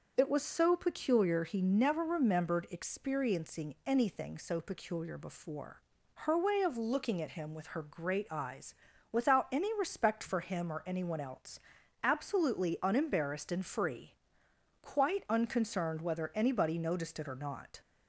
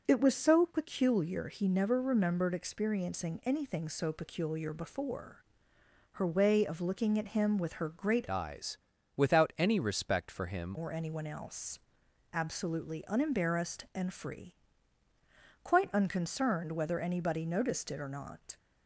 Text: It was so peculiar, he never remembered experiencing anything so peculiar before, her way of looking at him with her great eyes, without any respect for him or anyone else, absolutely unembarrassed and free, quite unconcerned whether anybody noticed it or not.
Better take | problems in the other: first | starts louder than the rest; until 1.0 s; 6.5 dB; noticeable in the first // changes voice from "eyes" to "him"; from 8.2 to 10.7 s; 2.5 s long

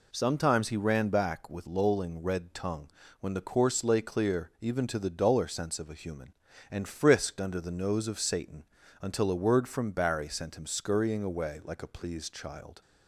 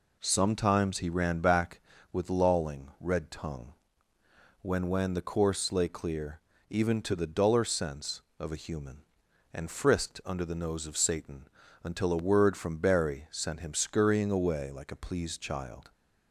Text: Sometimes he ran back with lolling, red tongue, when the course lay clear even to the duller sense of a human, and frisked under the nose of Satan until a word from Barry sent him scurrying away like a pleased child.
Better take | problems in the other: first | says "when" twice; at 4.8 s // pauses between "clear" and "even"; slight; at 6.3 s; 0.32 s long // pauses between "Satan" and "until"; slight; at 11.4 s; 0.36 s long; also in the first

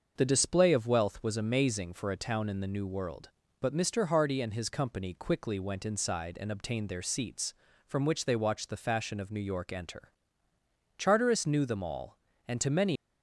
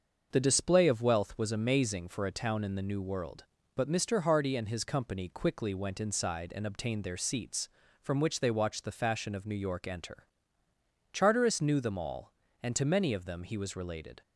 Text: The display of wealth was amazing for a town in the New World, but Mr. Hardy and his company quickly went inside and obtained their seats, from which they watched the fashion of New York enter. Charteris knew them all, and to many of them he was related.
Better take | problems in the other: second | starts louder than the rest; until 1.1 s; 6.5 dB; also in the second // stops before "of them he was related"; at 12.9 s

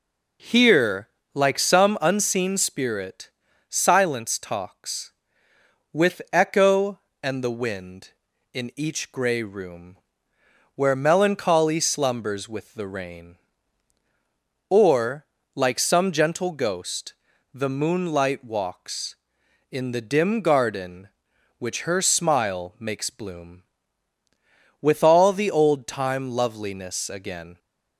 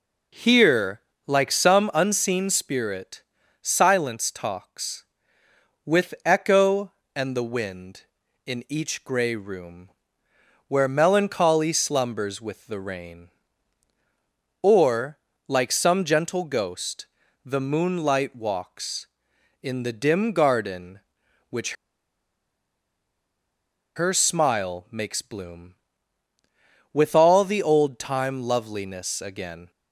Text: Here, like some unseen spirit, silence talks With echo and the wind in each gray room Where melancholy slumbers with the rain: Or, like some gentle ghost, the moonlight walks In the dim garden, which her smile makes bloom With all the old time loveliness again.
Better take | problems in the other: first | pauses between "room" and "Where"; noticeable; at 9.8 s; 0.78 s long; noticeable in the first // pauses between "which" and "her"; strong; at 21.7 s; 2.2 s long

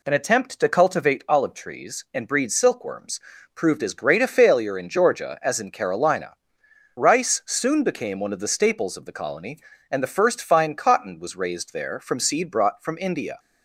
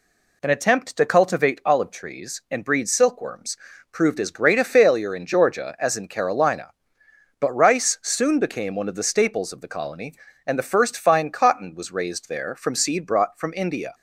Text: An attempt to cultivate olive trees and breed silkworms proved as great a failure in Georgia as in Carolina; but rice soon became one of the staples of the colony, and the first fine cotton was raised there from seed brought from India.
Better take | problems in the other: second | pauses between "silkworms" and "proved"; slight; at 3.2 s; 0.34 s long; slight in the second // skips "but"; at 6.6 s

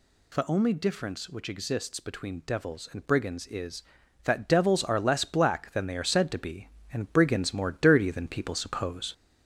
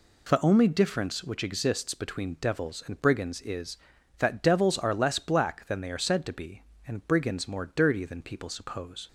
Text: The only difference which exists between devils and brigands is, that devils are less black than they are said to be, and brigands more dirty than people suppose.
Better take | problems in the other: second | gets louder; slight; throughout; 2 dB

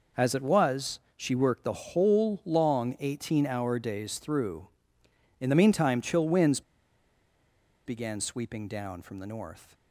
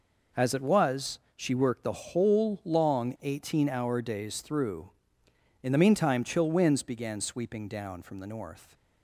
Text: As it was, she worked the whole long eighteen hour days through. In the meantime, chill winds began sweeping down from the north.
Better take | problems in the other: second | pauses between "winds" and "began"; strong; at 6.6 s; 1.2 s long

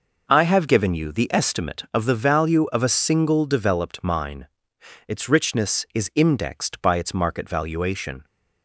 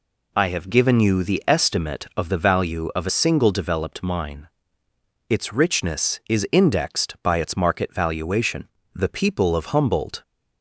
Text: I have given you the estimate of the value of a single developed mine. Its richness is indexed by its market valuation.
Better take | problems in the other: first | goes on to say "The people of Humboldt"; noticeable; from 8.9 s on; 1.2 s long

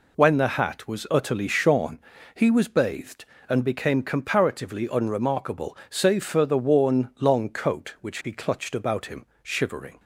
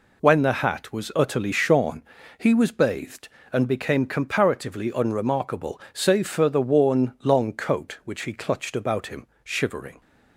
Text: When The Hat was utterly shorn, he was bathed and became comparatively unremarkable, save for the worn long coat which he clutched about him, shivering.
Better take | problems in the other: neither | none

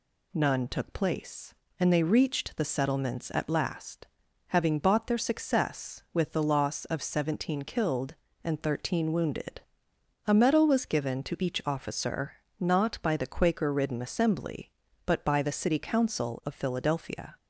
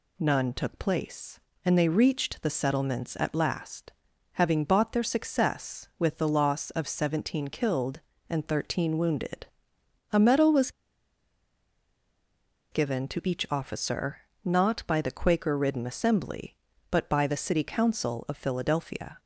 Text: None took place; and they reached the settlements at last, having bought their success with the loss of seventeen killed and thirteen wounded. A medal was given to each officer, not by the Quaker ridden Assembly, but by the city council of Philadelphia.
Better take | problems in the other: first | pauses between "was" and "given"; strong; at 10.6 s; 2.0 s long

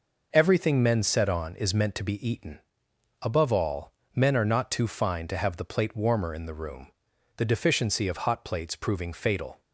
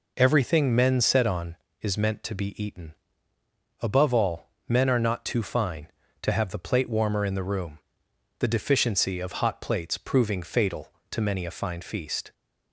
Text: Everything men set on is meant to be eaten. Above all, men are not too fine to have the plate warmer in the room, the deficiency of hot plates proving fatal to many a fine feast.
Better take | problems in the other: second | stops before "to many a fine feast"; at 9.6 s

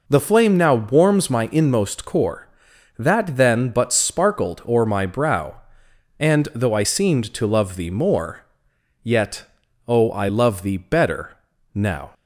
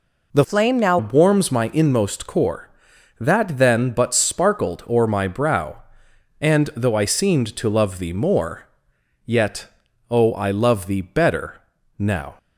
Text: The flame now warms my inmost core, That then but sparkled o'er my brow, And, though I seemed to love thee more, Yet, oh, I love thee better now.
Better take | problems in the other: first | changes voice from "flame" to "now"; from 0.4 to 0.9 s; 0.5 s long // pauses between "better" and "now"; slight; at 11.6 s; 0.36 s long; slight in the first

